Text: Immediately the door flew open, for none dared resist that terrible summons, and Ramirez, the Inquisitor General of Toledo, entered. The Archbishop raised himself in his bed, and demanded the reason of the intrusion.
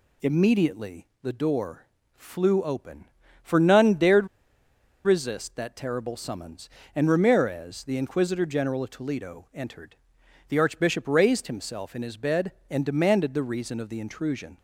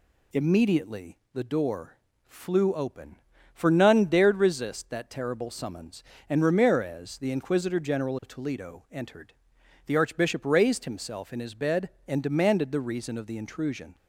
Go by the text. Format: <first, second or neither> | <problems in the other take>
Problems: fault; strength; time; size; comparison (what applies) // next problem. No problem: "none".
second | pauses between "Immediately" and "the"; slight; at 1.0 s; 0.16 s long; slight in the second // pauses between "door" and "flew"; slight; at 1.8 s; 0.28 s long; slight in the second // pauses between "dared" and "resist"; noticeable; at 4.2 s; 0.77 s long